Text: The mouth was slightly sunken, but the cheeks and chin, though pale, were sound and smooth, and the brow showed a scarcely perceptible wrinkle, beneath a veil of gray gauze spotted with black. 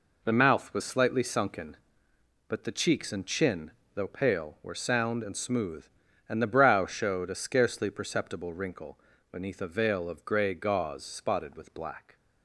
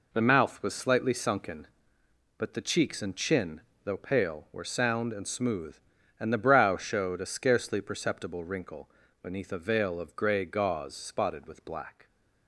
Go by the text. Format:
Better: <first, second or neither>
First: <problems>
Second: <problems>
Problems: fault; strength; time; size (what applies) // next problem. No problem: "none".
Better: neither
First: none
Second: none